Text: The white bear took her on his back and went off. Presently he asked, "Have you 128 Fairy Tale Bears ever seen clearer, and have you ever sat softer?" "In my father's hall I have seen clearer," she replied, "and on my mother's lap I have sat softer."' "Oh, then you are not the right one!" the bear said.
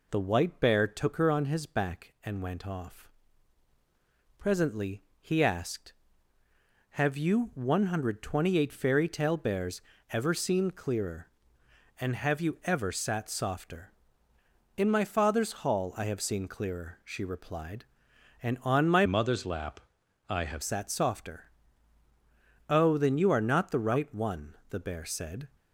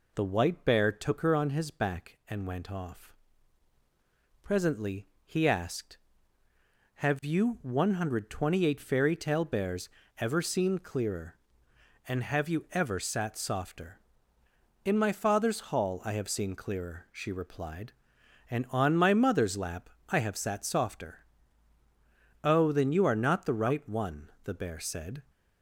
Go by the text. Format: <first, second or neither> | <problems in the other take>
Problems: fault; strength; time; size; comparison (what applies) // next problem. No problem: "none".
second | pauses between "Presently" and "he"; slight; at 5.0 s; 0.18 s long; slight in the second // pauses between "Bears" and "ever"; slight; at 9.8 s; 0.28 s long; slight in the second // changes voice from "mother's" to "have"; from 19.0 to 20.6 s; 1.6 s long // pauses between "lap" and "I"; noticeable; at 19.7 s; 0.50 s long; slight in the second